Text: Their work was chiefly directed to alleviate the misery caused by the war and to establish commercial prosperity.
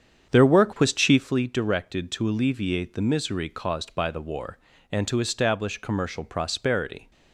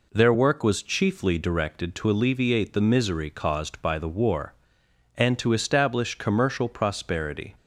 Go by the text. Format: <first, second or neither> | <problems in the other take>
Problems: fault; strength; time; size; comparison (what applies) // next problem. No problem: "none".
second | starts louder than the rest; strong; until 1.4 s; 8 dB